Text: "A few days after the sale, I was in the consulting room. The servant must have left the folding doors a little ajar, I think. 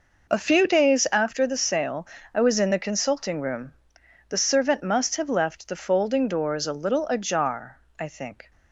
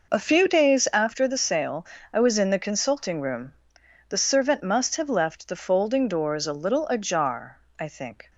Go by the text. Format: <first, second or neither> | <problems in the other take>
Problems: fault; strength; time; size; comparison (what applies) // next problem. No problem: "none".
neither | none